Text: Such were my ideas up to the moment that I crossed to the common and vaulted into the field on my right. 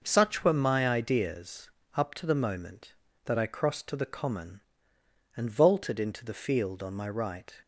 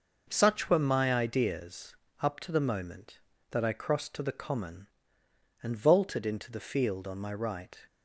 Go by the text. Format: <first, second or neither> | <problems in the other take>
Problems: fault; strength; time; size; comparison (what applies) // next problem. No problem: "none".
neither | pauses between "ideas" and "up"; slight; the same in both